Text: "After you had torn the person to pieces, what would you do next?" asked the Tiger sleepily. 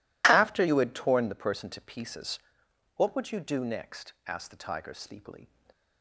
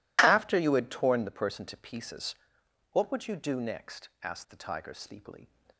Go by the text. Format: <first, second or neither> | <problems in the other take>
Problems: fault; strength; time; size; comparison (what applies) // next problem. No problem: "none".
neither | none